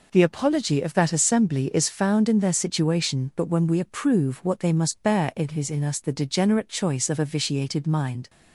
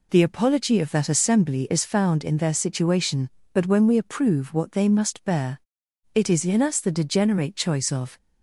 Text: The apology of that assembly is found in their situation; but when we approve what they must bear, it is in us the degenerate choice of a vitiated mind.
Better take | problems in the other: first | stops before "a vitiated mind"; at 8.1 s

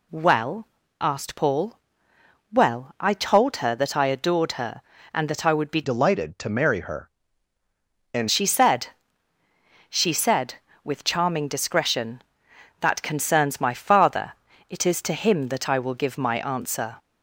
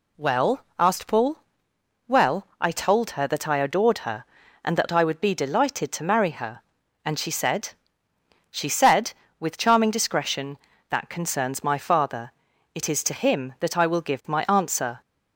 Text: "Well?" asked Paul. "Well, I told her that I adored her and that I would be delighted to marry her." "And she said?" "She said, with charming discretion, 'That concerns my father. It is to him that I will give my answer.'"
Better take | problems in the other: second | changes voice from "delighted" to "And"; from 5.8 to 8.2 s; 2.4 s long

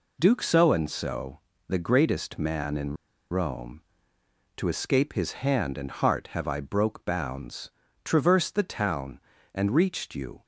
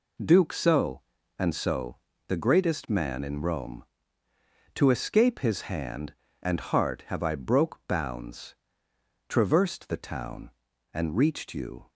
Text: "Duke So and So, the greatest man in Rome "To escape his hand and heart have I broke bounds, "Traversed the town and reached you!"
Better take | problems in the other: second | pauses between "in" and "Rome"; at 2.9 s; 0.37 s long

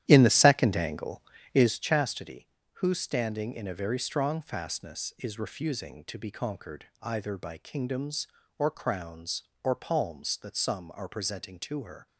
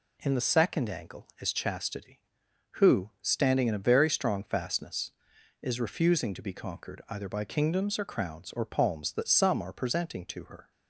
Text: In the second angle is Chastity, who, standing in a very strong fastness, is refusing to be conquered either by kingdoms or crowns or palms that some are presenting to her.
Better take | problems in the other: second | starts louder than the rest; strong; until 1.8 s; 12 dB // pauses between "conquered" and "either"; slight; at 6.8 s; 0.16 s long

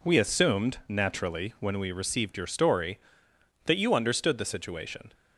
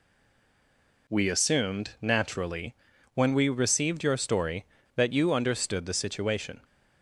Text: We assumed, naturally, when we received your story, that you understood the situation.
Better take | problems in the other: first | stays silent before the first word; until 1.0 s; 1.0 s long

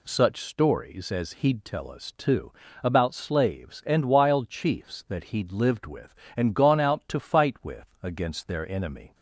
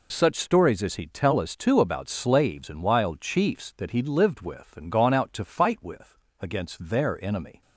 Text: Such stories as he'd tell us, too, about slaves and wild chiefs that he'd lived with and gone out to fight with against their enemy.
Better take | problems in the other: neither | pauses between "with" and "against"; slight; the same in both

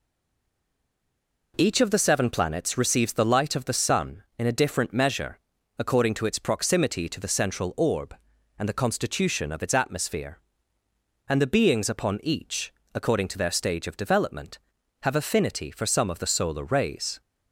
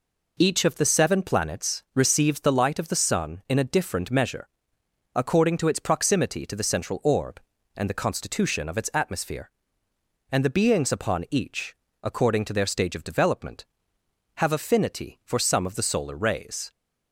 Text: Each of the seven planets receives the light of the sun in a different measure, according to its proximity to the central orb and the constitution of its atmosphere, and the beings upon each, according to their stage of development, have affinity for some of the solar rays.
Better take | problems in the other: second | stays silent before the first word; noticeable; until 1.5 s; 1.5 s long

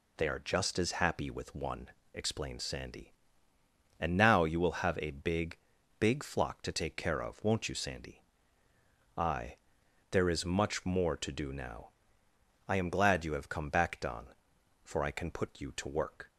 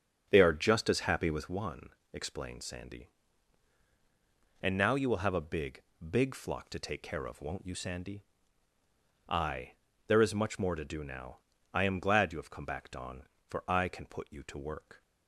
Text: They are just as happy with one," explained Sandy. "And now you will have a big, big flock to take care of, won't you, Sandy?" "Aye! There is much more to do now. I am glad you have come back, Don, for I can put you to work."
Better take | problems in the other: first | starts louder than the rest; strong; until 1.6 s; 7.5 dB

